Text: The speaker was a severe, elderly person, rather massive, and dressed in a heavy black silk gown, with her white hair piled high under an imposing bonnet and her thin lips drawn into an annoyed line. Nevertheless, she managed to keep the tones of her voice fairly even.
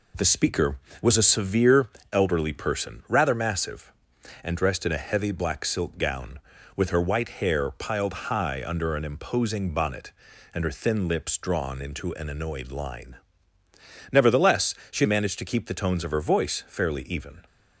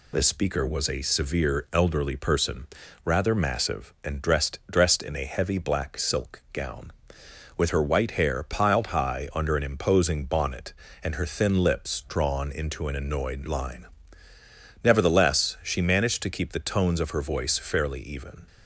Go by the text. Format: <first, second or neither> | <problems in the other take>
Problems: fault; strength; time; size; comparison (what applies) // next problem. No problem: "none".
first | says "dressed" twice; at 4.7 s